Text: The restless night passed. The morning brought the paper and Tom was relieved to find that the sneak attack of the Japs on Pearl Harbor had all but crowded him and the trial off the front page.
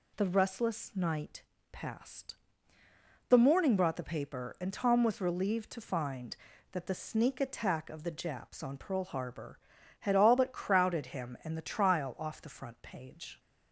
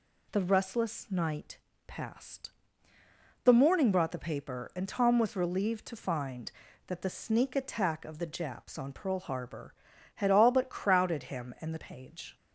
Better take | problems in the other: first | pauses between "night" and "passed"; slight; at 1.5 s; 0.30 s long; slight in the first // skips "trial off the front"; at 11.7 s

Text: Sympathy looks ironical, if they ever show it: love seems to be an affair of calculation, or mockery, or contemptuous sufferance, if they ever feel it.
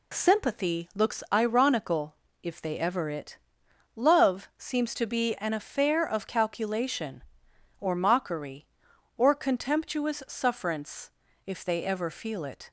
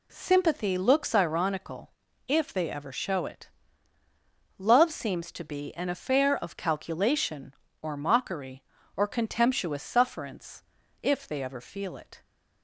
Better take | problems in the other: second | skips "show"; at 3.0 s

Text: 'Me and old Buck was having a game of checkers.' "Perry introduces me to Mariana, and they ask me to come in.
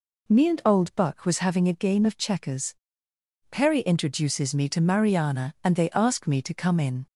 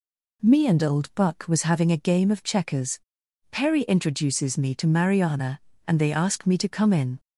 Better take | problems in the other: neither | none

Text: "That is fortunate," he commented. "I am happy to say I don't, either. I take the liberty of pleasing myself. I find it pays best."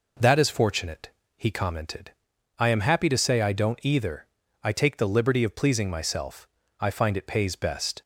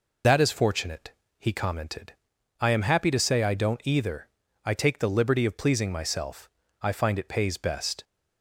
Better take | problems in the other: first | loses the start of "That"; at 0.2 s; 65 ms

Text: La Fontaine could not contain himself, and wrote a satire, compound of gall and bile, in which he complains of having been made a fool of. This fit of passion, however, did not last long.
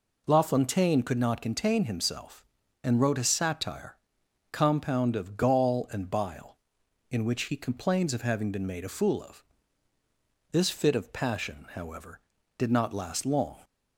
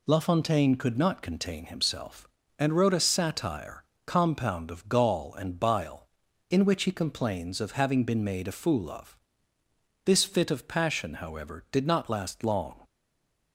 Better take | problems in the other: first | stays silent after the last word; slight; from 12.8 s on; 0.7 s long

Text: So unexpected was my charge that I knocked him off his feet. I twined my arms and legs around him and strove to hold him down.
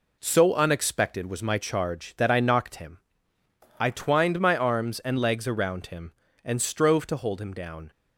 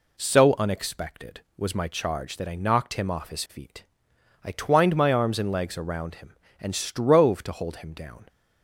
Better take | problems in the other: second | skips "off his feet"; at 3.3 s

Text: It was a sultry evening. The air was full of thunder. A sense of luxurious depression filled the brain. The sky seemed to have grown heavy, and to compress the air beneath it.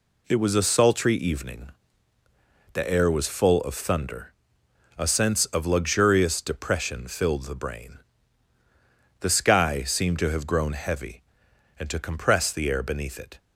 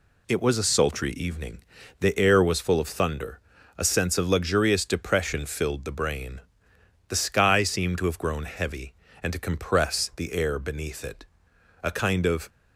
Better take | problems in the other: first | goes on to say "A kind of"; noticeable; from 11.8 s on; 0.66 s long

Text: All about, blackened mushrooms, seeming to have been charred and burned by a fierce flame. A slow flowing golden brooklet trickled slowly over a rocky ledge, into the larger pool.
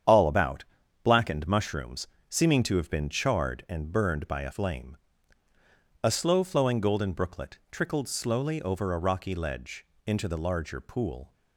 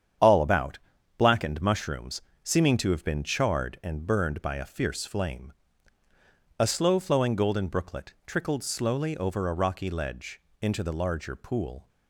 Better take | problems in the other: second | starts louder than the rest; strong; until 1.4 s; 8.5 dB; strong in the second // skips "fierce"; at 4.5 s

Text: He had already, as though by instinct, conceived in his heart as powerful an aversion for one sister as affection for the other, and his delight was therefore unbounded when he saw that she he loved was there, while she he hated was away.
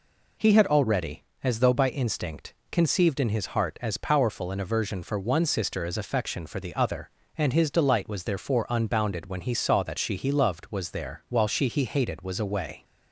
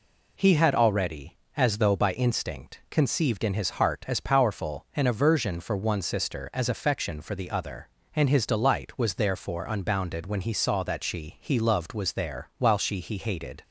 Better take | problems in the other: first | stops before "was away"; at 13.6 s

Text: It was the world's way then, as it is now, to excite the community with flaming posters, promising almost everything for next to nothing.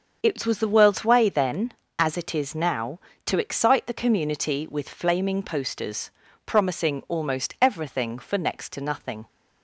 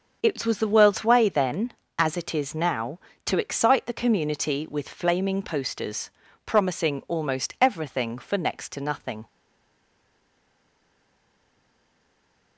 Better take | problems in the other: first | starts louder than the rest; until 1.2 s; 7 dB; also in the first // stays silent after the last word; strong; from 9.2 s on; 3.3 s long

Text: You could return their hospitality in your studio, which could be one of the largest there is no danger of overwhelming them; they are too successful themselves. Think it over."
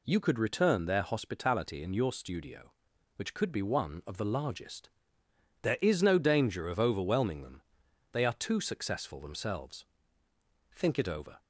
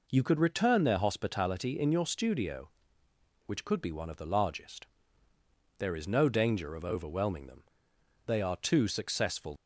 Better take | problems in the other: first | pauses between "largest" and "there"; noticeable; at 4.8 s; 0.92 s long; noticeable in the first // stops before "themselves Think it over"; at 9.5 s

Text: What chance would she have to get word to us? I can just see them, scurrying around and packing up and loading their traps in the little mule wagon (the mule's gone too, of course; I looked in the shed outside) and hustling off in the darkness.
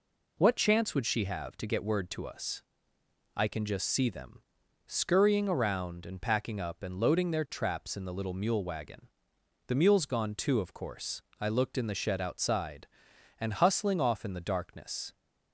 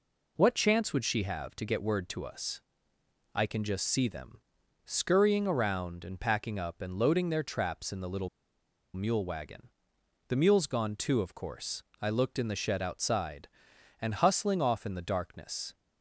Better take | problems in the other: first | pauses between "little" and "mule"; noticeable; at 8.2 s; 0.65 s long

